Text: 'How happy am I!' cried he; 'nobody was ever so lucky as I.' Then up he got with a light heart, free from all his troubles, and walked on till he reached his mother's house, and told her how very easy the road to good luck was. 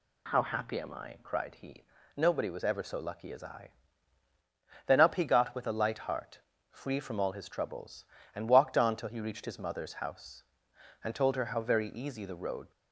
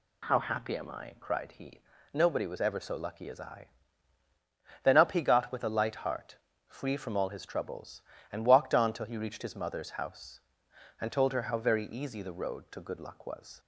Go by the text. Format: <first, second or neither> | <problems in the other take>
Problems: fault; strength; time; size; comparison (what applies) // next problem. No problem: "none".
second | stops before "to good luck was"; at 12.7 s